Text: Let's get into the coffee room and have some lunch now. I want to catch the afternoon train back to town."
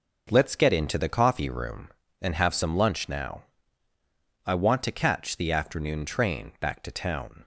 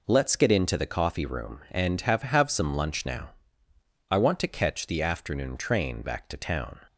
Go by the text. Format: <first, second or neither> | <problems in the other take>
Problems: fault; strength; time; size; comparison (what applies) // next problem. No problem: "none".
first | says "have" twice; at 2.2 s